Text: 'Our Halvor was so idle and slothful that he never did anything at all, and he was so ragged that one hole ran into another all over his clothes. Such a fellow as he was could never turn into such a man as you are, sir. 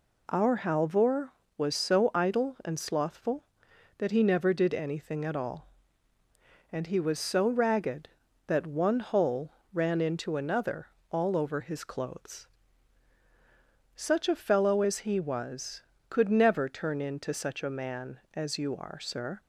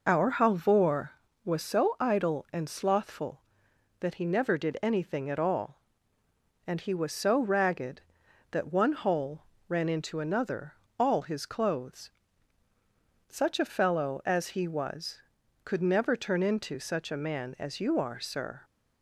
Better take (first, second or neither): first